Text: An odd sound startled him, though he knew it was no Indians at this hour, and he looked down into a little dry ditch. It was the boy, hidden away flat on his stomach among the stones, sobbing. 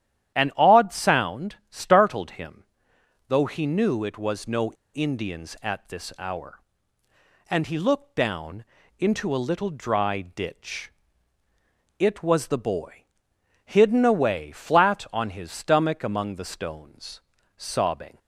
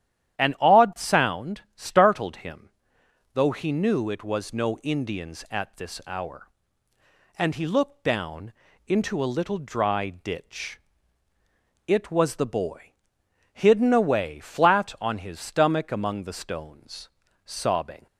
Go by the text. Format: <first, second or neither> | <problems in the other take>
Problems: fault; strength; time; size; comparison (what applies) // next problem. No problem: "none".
second | starts louder than the rest; strong; until 1.3 s; 10.5 dB; strong in the second // pauses between "no" and "Indians"; slight; at 4.7 s; 0.22 s long // pauses between "down" and "into"; slight; at 8.6 s; 0.34 s long; slight in the second